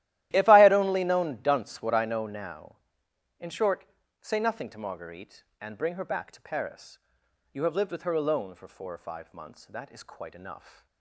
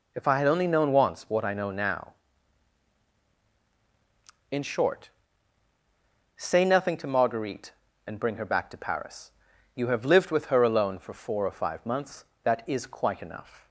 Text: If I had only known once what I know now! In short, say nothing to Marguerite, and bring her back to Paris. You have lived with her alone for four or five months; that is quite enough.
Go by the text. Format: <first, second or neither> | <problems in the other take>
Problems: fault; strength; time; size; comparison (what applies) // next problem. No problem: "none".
second | starts louder than the rest; strong; until 1.3 s; 14.5 dB // says "dunce" for "once"; at 1.4 s